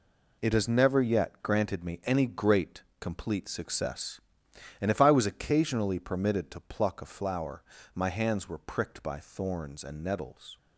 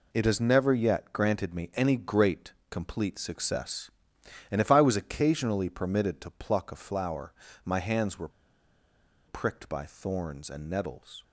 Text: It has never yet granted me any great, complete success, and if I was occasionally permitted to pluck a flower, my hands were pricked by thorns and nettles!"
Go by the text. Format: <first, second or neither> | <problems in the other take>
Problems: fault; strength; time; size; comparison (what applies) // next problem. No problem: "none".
first | pauses between "were" and "pricked"; at 8.2 s; 0.98 s long